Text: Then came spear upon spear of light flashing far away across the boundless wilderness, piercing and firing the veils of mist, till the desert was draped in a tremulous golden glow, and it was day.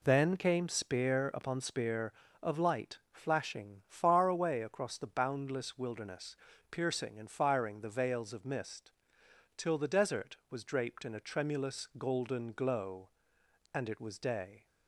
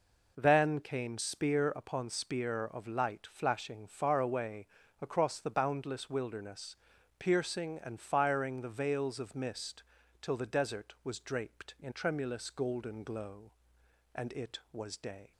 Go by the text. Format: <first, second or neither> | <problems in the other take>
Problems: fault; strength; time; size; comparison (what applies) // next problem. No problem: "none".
first | pauses between "away" and "across"; slight; at 4.6 s; 0.34 s long // skips "a"; at 11.9 s